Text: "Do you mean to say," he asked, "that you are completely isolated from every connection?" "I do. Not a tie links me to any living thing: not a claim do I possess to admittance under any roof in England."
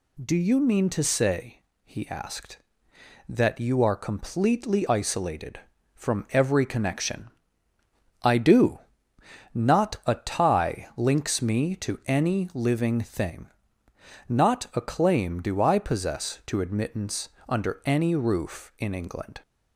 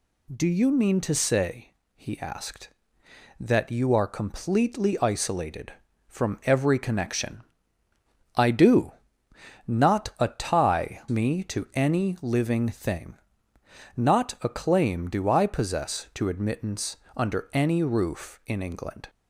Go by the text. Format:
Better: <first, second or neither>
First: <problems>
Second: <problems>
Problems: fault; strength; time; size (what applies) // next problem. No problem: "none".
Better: first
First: pauses between "admittance" and "under"; slight; at 17.2 s; 0.22 s long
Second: skips "links"; at 11.0 s // pauses between "admittance" and "under"; slight; at 16.9 s; 0.22 s long